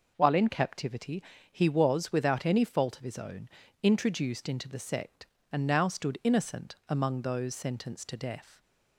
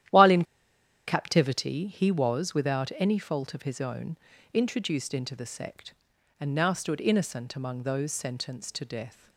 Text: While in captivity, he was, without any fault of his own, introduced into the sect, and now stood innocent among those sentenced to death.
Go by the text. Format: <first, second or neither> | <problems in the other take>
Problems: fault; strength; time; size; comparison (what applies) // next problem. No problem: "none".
first | starts louder than the rest; strong; until 1.7 s; 12 dB // pauses between "in" and "captivity"; noticeable; at 0.4 s; 0.62 s long